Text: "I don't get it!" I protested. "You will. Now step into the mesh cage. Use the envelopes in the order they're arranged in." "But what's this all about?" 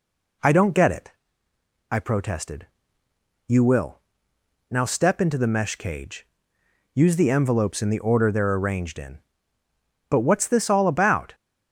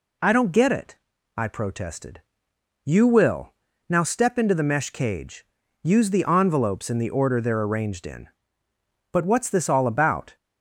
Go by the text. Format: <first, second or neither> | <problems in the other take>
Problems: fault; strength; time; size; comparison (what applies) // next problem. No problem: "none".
neither | none